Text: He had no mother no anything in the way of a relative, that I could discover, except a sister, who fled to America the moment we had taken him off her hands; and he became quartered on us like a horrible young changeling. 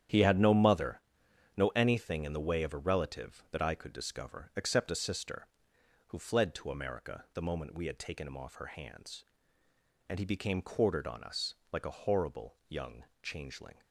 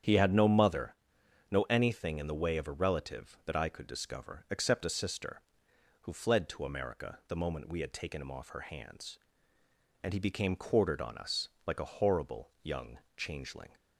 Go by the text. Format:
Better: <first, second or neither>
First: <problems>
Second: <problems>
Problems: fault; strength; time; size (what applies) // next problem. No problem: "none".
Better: second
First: gets quieter; strong; throughout; 9.5 dB // starts louder than the rest; strong; until 1.6 s; 10 dB // pauses between "mother" and "no"; noticeable; at 1.0 s; 0.54 s long // pauses between "us" and "like"; slight; at 11.5 s; 0.16 s long // pauses between "young" and "changeling"; slight; at 13.0 s; 0.18 s long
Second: starts louder than the rest; strong; until 1.5 s; 9 dB // pauses between "mother" and "no"; noticeable; at 0.9 s; 0.54 s long // pauses between "us" and "like"; slight; at 11.4 s; 0.16 s long // pauses between "young" and "changeling"; slight; at 12.9 s; 0.18 s long